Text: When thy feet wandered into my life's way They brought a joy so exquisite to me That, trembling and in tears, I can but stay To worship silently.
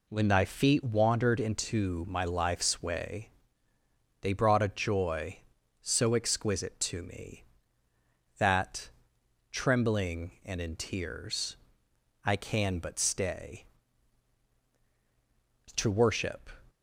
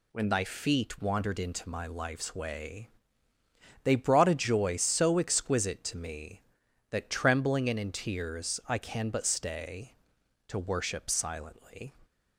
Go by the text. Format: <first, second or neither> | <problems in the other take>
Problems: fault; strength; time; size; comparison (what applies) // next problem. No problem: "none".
second | pauses between "way" and "They"; noticeable; at 3.2 s; 0.92 s long; noticeable in the second // stops before "silently"; at 16.6 s